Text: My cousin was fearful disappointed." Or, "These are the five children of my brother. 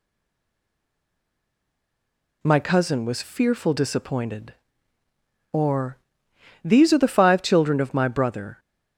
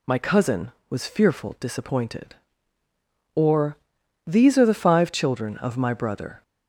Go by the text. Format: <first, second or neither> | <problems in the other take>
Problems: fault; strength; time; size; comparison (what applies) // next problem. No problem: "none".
second | stays silent before the first word; until 2.4 s; 2.4 s long